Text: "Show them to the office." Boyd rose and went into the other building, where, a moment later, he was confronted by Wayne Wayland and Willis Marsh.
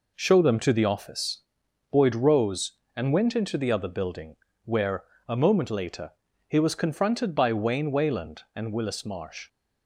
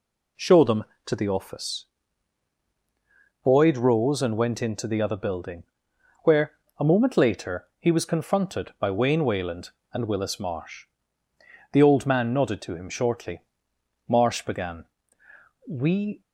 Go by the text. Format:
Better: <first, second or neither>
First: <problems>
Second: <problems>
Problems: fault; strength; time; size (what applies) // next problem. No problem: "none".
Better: first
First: none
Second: goes on to say "The old man nodded to him shortly Marsh began We"; strong; from 11.7 s on; 4.5 s long